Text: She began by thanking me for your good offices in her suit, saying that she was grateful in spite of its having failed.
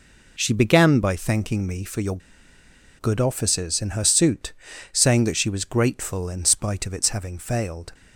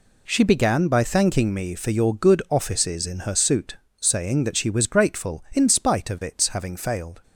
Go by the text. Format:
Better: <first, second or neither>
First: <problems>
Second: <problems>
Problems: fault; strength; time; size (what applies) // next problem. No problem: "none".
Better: second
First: pauses between "your" and "good"; noticeable; at 2.1 s; 0.79 s long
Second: none